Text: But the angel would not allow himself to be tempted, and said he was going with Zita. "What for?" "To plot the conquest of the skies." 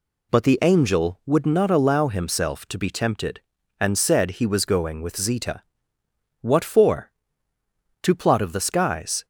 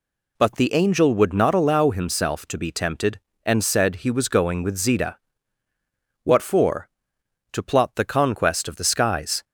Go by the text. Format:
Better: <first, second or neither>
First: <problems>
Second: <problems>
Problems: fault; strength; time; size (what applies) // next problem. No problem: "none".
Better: second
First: skips "the conquest"; at 8.3 s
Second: none